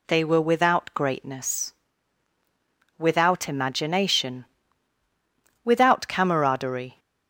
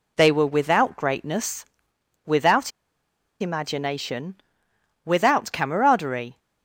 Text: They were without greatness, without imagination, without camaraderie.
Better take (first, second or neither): first